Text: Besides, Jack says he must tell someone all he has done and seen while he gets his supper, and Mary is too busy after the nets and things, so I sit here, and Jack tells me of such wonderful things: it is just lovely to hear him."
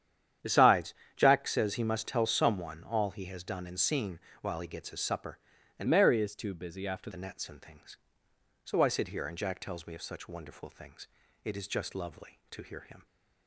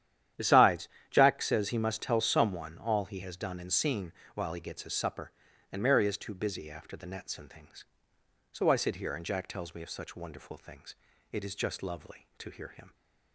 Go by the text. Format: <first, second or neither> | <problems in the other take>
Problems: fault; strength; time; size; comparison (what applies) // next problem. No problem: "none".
second | starts louder than the rest; strong; until 1.6 s; 9.5 dB; strong in the second // pauses between "seen" and "while"; slight; at 4.1 s; 0.22 s long; slight in the second // changes voice from "Mary" to "after"; from 5.8 to 7.1 s; 1.3 s long